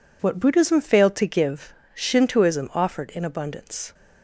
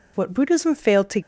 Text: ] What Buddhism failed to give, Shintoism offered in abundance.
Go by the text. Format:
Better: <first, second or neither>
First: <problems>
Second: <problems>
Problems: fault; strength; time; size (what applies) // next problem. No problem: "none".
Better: first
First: none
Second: stops before "give Shintoism offered in abundance"; at 1.2 s